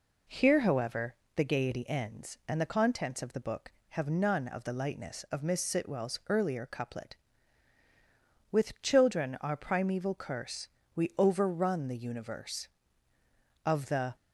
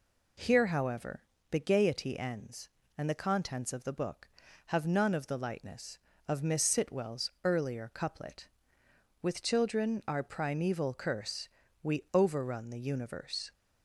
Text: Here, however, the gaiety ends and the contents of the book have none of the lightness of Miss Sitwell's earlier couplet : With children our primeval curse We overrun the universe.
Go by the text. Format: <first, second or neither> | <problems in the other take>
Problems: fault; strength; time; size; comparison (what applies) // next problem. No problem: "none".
second | pauses between "curse" and "We"; slight; at 10.6 s; 0.26 s long; slight in the second // goes on to say "Of the"; from 13.6 s on; 0.50 s long